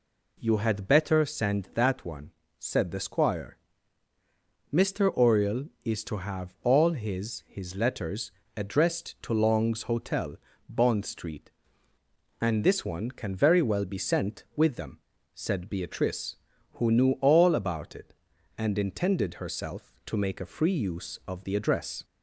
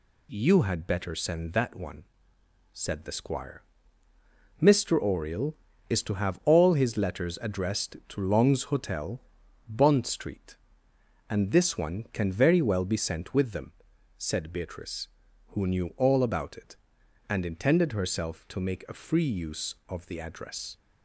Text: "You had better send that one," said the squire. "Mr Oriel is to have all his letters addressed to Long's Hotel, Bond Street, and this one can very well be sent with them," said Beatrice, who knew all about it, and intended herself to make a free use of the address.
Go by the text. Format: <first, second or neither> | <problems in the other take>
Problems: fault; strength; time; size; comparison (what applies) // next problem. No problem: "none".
second | says "his" twice; at 7.4 s // pauses between "letters" and "addressed"; slight; at 8.3 s; 0.26 s long